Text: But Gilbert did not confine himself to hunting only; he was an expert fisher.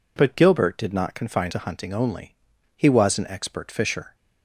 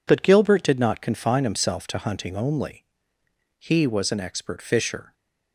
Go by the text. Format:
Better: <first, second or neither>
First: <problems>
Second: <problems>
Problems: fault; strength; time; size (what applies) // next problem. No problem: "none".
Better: second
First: skips "himself"; at 1.5 s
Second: none